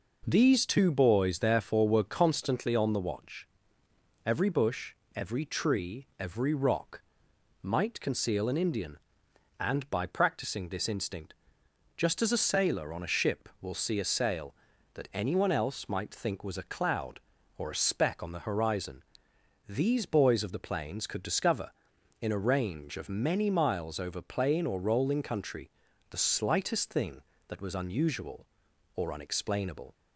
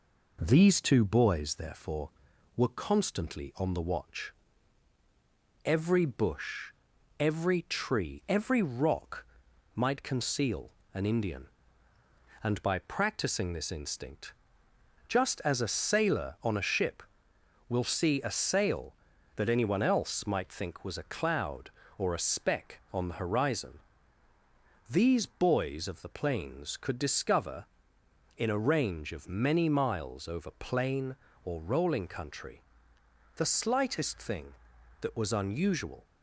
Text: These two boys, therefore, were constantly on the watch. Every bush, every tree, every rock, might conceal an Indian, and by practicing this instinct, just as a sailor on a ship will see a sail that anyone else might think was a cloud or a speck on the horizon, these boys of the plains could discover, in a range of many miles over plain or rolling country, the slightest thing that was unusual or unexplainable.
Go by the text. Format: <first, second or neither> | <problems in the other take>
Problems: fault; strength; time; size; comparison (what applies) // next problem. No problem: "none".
first | pauses between "conceal" and "an"; slight; at 10.7 s; 0.22 s long // stops before "or unexplainable"; at 36.0 s